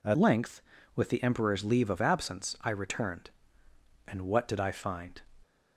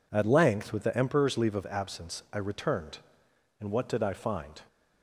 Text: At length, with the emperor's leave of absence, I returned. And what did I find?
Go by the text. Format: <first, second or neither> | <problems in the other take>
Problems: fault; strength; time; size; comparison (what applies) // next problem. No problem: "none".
second | changes voice at "length"; from 0.1 s on; 5.1 s long